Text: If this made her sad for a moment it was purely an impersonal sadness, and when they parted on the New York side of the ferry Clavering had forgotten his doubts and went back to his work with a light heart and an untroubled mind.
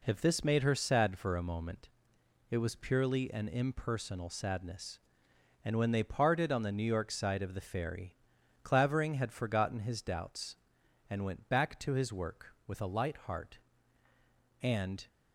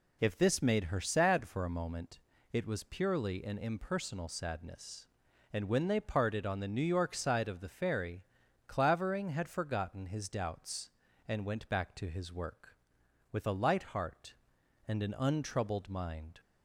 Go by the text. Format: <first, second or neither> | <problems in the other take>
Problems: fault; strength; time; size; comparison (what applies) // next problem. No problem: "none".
second | pauses between "moment" and "it"; noticeable; at 1.8 s; 0.62 s long; slight in the second // pauses between "ferry" and "Clavering"; noticeable; at 8.1 s; 0.50 s long; also in the second // stops before "an untroubled mind"; at 15.0 s